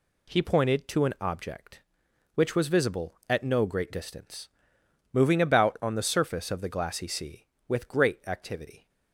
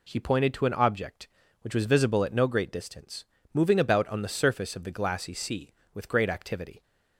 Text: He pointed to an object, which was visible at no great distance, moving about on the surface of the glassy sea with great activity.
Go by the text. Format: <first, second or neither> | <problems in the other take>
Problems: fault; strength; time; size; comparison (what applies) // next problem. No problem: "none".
neither | none